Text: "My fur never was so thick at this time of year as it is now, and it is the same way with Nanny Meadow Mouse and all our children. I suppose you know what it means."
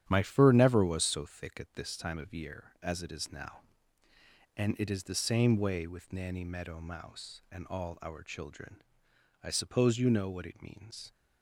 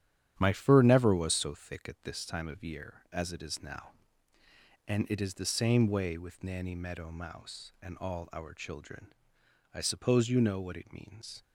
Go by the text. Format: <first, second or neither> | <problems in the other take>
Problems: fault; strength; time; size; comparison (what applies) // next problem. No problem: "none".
neither | starts louder than the rest; strong; the same in both